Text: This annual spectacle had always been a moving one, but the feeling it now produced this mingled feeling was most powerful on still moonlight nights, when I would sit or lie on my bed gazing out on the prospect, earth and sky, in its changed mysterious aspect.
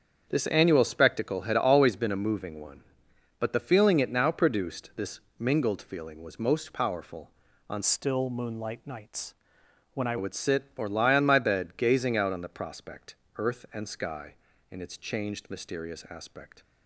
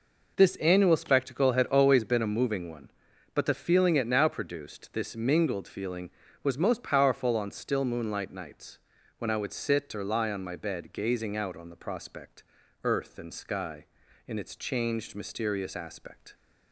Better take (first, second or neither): second